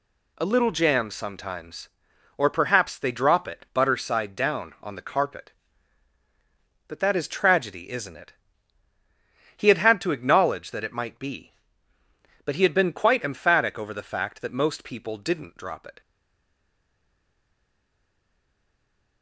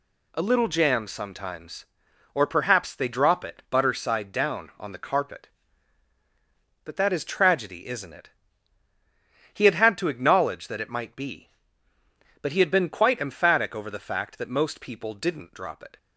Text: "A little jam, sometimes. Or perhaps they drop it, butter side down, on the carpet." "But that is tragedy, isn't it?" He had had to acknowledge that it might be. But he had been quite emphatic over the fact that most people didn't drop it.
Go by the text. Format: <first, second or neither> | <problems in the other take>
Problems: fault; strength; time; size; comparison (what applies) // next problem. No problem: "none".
second | stays silent after the last word; strong; from 16.0 s on; 3.2 s long